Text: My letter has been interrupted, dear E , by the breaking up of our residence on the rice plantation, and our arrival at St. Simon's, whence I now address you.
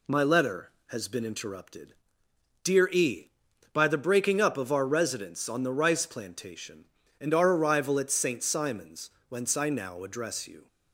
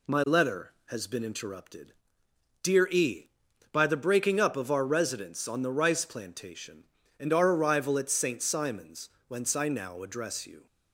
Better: neither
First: none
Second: none

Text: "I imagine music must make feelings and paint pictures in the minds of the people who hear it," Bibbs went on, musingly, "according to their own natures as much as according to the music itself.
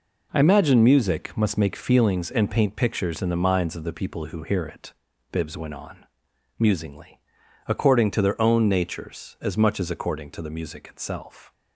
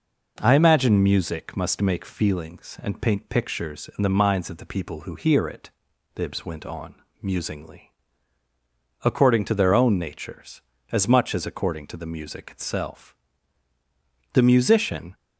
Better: first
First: none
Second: goes on to say "The musician"; noticeable; from 14.3 s on; 0.82 s long

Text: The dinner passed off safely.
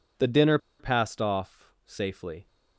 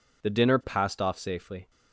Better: second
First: pauses between "dinner" and "passed"; slight; at 0.5 s; 0.22 s long // pauses between "off" and "safely"; slight; at 1.6 s; 0.18 s long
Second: none

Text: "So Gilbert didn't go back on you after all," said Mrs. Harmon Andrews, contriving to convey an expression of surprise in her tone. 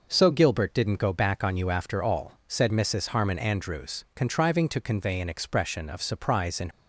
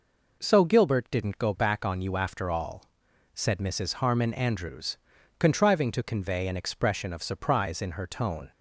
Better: second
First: stops before "her tone"; at 6.7 s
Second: none

